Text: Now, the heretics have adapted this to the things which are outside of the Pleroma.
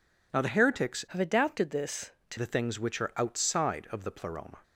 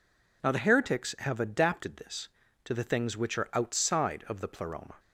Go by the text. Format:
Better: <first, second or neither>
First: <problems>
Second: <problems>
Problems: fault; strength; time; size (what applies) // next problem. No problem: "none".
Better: second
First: changes voice from "have" to "to"; from 1.0 to 2.3 s; 1.3 s long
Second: none